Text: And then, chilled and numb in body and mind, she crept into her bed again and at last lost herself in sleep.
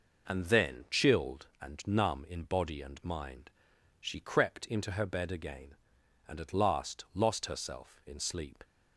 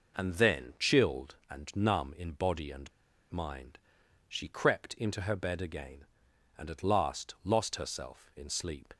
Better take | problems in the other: first | pauses between "and" and "mind"; at 2.9 s; 0.40 s long

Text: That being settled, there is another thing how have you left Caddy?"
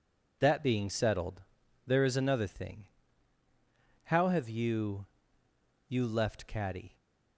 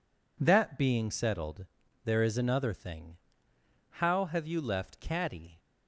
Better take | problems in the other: second | pauses between "thing" and "how"; at 2.8 s; 1.2 s long; noticeable in the second // says "you" twice; at 5.8 s

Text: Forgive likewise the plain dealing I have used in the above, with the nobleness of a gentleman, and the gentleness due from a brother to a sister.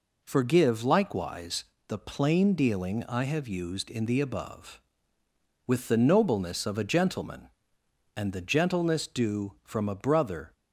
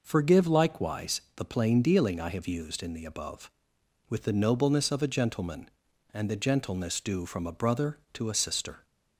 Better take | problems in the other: second | pauses between "likewise" and "the"; slight; at 1.6 s; 0.24 s long; slight in the second // stops before "to a sister"; at 10.5 s

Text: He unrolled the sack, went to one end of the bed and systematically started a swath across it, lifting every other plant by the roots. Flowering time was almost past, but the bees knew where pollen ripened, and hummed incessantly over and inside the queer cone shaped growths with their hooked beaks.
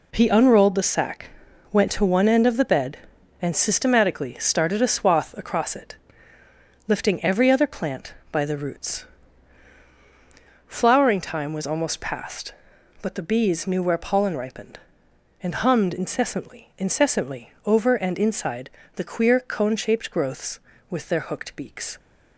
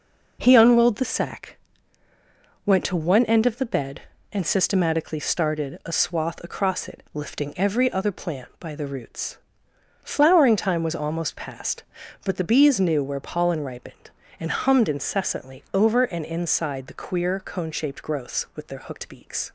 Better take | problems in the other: second | says "incessantly" twice; at 16.7 s // pauses between "inside" and "the"; slight; at 18.6 s; 0.28 s long

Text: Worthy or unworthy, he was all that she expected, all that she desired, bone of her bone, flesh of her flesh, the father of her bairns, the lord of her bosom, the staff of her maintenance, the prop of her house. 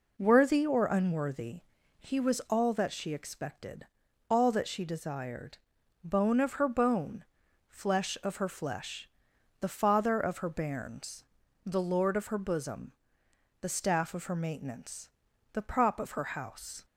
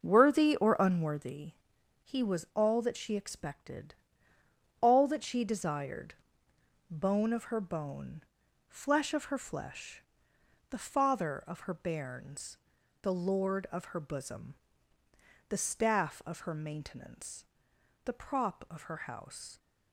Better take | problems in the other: first | starts louder than the rest; until 1.4 s; 6 dB

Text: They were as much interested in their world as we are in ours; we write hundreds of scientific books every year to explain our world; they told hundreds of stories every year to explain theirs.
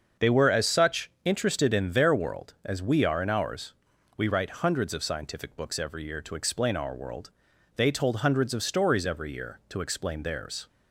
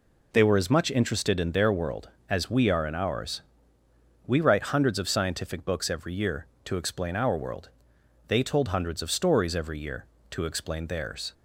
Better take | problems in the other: second | starts louder than the rest; until 1.3 s; 6.5 dB // says "such" for "much"; at 0.6 s

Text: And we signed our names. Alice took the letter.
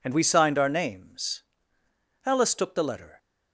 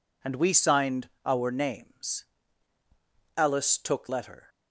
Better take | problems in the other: first | pauses between "signed" and "our"; slight; at 1.0 s; 0.16 s long // skips "the"; at 4.0 s

